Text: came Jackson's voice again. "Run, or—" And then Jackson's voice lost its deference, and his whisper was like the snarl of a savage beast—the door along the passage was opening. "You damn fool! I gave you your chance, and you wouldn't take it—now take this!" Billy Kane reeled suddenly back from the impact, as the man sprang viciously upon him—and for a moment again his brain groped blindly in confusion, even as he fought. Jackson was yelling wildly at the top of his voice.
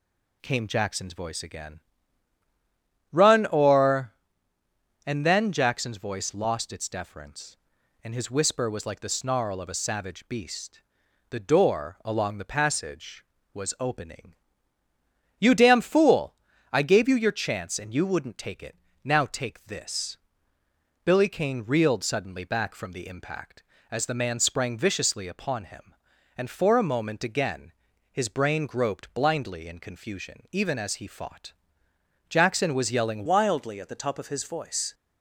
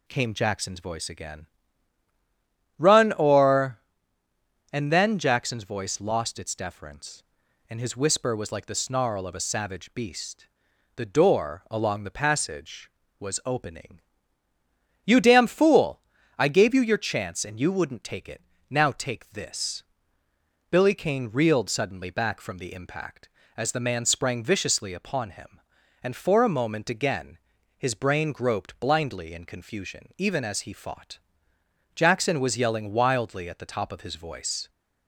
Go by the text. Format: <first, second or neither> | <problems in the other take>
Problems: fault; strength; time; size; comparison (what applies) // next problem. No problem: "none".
second | pauses between "again" and "his"; at 27.7 s; 0.38 s long; also in the second // changes voice at "wildly"; from 33.2 s on; 1.7 s long